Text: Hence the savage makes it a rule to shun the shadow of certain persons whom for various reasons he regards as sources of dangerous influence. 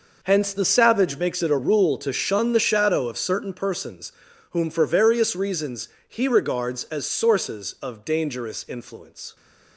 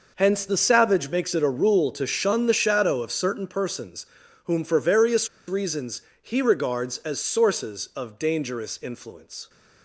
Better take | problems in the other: first | pauses between "persons" and "whom"; at 4.0 s; 0.38 s long; also in the first // pauses between "various" and "reasons"; slight; at 5.2 s; 0.19 s long // pauses between "reasons" and "he"; slight; at 6.0 s; 0.20 s long; slight in the first

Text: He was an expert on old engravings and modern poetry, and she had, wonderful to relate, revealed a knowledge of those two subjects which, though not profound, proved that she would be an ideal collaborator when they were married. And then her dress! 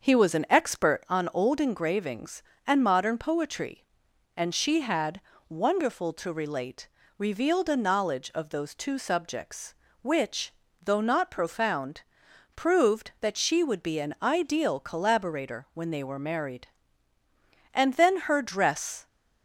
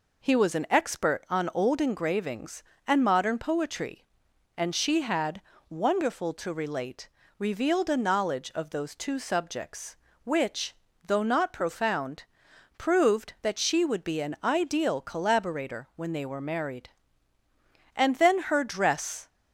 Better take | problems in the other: second | starts louder than the rest; until 1.2 s; 6.5 dB

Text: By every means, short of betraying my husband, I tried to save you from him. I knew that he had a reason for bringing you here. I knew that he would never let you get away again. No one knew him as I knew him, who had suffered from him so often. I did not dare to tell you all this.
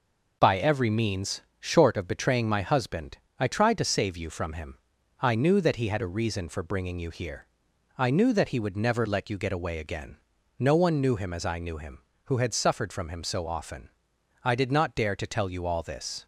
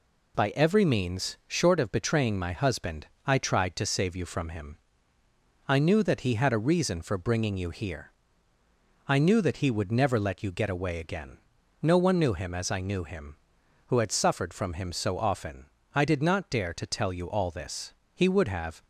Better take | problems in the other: first | goes on to say "He would have"; noticeable; from 18.1 s on; 0.68 s long

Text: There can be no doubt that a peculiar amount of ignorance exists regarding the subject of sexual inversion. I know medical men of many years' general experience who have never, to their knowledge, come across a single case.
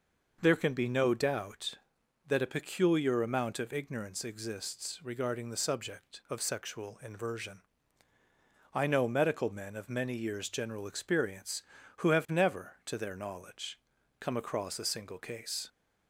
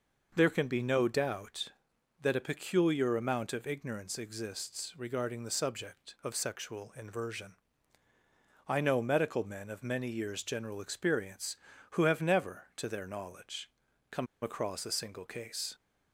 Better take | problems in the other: first | pauses between "come" and "across"; slight; at 14.2 s; 0.16 s long

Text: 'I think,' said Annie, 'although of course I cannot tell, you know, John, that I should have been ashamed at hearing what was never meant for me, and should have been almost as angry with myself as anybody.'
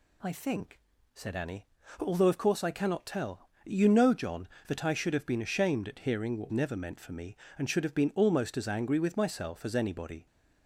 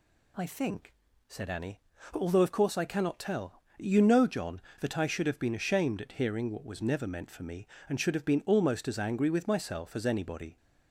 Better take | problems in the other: second | skips "was"; at 6.5 s

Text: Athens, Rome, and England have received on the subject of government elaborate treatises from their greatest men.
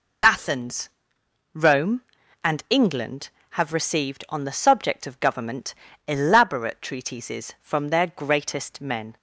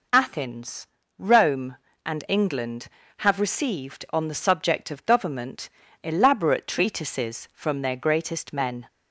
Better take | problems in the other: neither | pauses between "government" and "elaborate"; slight; the same in both

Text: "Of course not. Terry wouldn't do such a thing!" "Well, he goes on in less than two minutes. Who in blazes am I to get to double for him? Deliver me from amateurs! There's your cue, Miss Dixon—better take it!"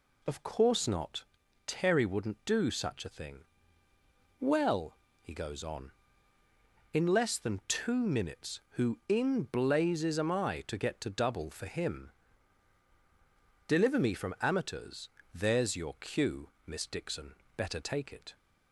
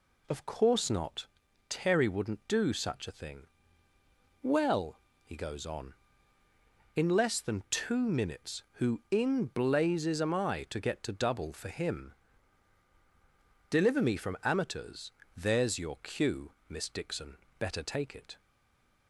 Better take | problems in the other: first | stays silent after the last word; slight; from 18.3 s on; 0.7 s long

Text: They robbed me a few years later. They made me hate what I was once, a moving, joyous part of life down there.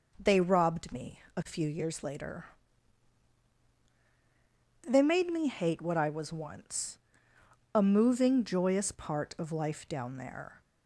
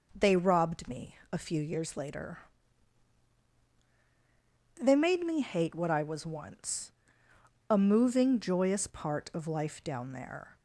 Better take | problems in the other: neither | pauses between "me" and "a"; slight; the same in both

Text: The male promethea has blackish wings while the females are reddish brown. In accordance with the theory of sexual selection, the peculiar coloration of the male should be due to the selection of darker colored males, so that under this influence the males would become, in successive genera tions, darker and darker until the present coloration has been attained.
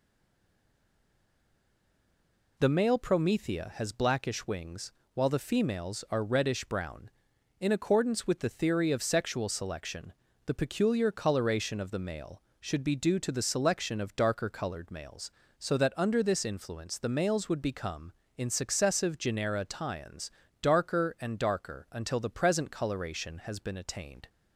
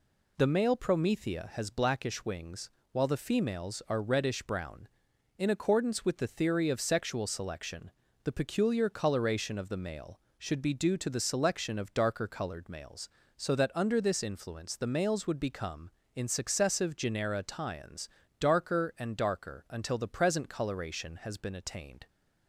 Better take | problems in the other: second | stays silent before the first word; strong; until 2.5 s; 2.5 s long // pauses between "wings" and "while"; slight; at 4.9 s; 0.22 s long; slight in the second

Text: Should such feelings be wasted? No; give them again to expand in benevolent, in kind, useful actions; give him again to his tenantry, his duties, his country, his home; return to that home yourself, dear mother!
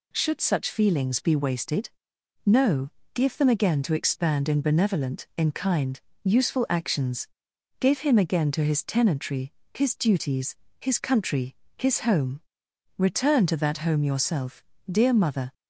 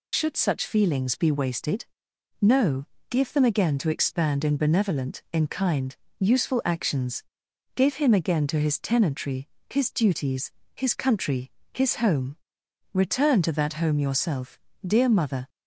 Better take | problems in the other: first | loses the start of "Should"; at 0.1 s; 45 ms

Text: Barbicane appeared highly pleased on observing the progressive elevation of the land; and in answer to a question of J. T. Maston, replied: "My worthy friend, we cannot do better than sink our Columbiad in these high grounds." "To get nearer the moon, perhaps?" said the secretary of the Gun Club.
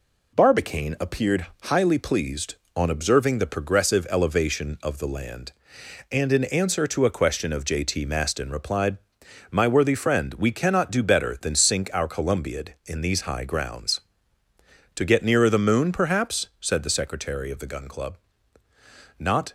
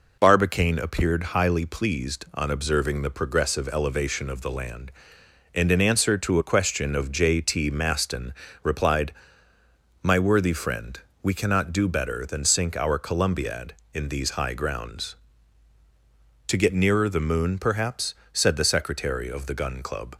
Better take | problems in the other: second | pauses between "appeared" and "highly"; slight; at 1.4 s; 0.18 s long // goes on to say "Not"; slight; from 19.1 s on; 0.34 s long

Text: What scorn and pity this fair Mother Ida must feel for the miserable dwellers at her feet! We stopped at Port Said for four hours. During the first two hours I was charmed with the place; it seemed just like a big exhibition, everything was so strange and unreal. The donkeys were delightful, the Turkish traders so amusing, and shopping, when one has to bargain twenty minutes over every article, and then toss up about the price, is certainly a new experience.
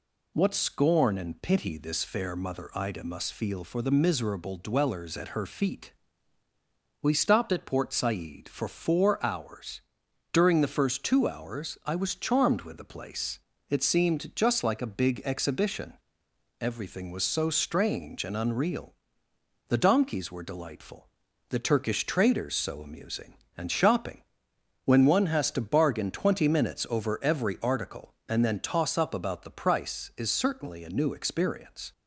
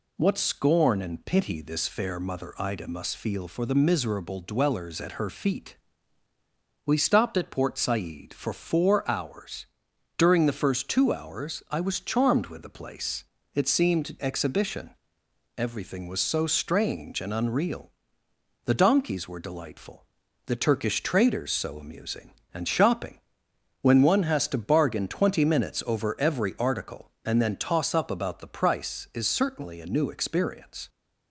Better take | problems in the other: first | skips "just like a big"; at 14.2 s

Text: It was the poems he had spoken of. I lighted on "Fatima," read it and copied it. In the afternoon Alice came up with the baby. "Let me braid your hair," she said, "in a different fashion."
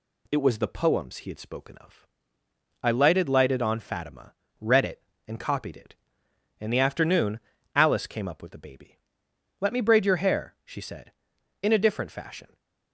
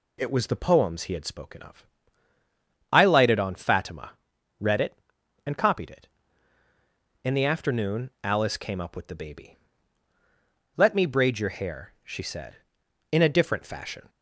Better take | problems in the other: second | says "lighted" twice; at 3.2 s // pauses between "afternoon" and "Alice"; slight; at 7.3 s; 0.36 s long

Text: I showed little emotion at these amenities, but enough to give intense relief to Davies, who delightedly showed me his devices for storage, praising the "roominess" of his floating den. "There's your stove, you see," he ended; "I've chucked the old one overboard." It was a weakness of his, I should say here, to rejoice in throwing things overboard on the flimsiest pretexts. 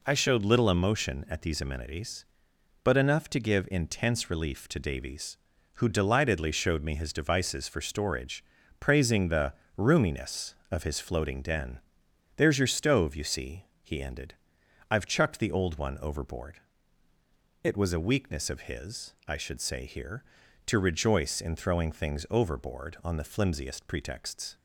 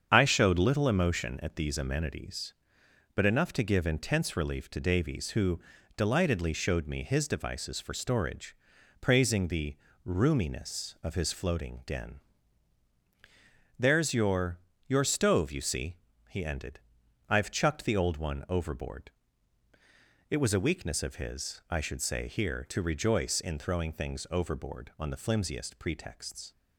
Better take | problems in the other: first | starts louder than the rest; strong; until 1.1 s; 7.5 dB // pauses between "who" and "delightedly"; at 5.5 s; 0.38 s long // pauses between "the" and "roominess"; slight; at 9.7 s; 0.30 s long; slight in the first // says "your" twice; at 14.8 s

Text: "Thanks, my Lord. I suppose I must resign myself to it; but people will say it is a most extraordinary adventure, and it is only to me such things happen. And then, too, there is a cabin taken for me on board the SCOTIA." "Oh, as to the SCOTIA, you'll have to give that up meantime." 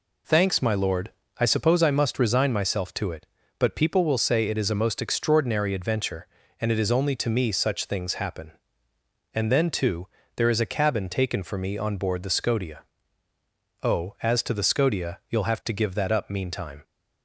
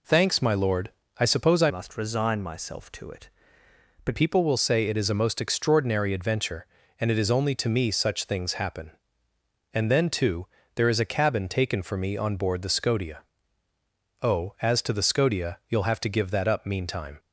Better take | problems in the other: first | changes voice from "must" to "but"; from 1.6 to 4.1 s; 2.5 s long

